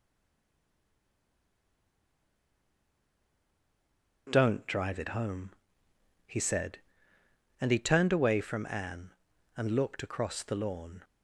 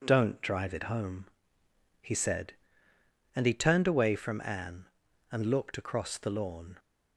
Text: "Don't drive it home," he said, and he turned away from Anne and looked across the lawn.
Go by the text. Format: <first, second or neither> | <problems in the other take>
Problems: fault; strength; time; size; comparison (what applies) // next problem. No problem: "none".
second | stays silent before the first word; strong; until 4.2 s; 4.2 s long